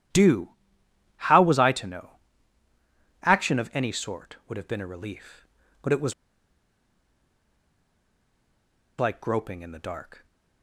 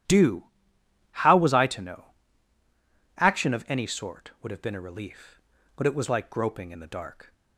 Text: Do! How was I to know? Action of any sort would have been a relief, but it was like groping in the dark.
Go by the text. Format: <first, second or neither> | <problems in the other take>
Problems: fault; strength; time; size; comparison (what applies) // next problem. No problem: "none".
second | starts louder than the rest; strong; until 1.7 s; 12 dB; strong in the second // pauses between "was" and "like"; strong; at 6.1 s; 2.8 s long